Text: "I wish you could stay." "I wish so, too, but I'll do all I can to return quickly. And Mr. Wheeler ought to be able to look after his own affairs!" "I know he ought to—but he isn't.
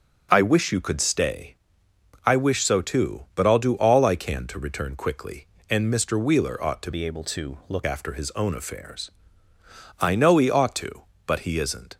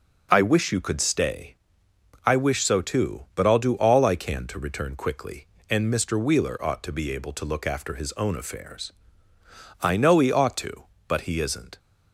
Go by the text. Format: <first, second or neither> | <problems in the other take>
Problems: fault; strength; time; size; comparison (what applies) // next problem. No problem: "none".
second | changes voice from "be" to "look"; from 6.9 to 7.8 s; 0.9 s long